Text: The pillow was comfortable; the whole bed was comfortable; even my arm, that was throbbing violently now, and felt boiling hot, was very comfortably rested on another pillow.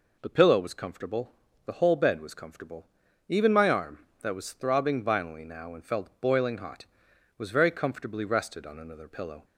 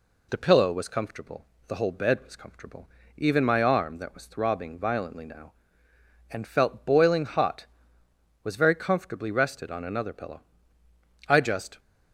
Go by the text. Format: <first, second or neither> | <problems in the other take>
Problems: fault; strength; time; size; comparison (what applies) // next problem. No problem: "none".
first | goes on to say "I just"; from 11.2 s on; 0.52 s long